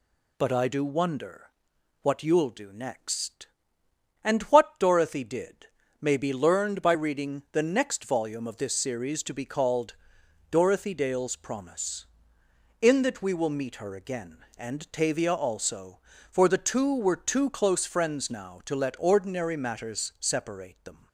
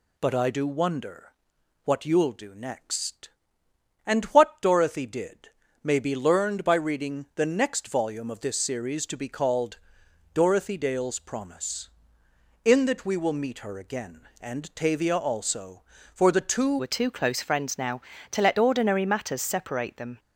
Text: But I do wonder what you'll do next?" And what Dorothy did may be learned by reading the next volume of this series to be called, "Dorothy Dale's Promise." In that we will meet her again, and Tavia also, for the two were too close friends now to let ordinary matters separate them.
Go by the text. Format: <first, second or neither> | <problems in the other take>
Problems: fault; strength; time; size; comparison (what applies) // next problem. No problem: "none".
first | pauses between "wonder" and "what"; noticeable; at 1.3 s; 0.52 s long; noticeable in the first // pauses between "did" and "may"; slight; at 5.4 s; 0.34 s long; slight in the first // changes voice at "were"; from 16.7 s on; 3.4 s long